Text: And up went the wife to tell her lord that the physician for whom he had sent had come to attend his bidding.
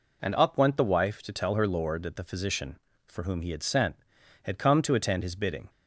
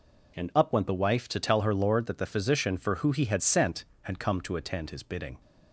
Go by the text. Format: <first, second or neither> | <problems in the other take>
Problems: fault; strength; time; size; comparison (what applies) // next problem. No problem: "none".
first | says "who" for "whom"; at 2.9 s